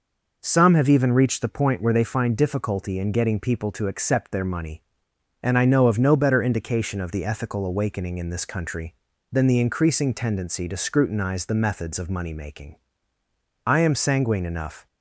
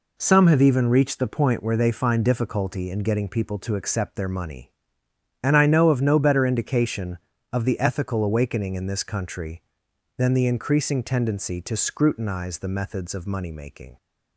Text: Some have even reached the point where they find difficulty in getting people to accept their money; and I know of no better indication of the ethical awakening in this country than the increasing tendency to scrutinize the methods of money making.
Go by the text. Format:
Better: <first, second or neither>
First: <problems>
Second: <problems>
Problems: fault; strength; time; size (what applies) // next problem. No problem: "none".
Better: second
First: goes on to say "I am sanguine enough"; noticeable; from 13.6 s on; 1.2 s long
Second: none